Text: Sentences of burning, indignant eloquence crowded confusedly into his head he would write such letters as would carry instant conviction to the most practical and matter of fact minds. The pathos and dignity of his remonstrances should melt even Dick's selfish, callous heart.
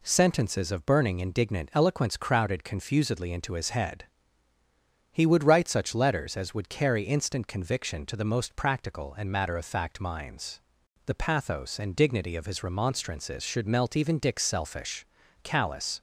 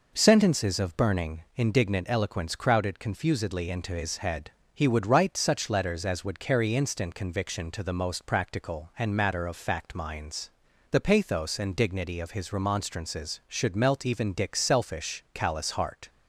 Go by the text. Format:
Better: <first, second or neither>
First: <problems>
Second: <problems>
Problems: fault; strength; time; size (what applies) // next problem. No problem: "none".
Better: second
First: pauses between "head" and "he"; at 4.0 s; 1.1 s long // stops before "heart"; at 15.9 s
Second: pauses between "head" and "he"; slight; at 4.5 s; 0.24 s long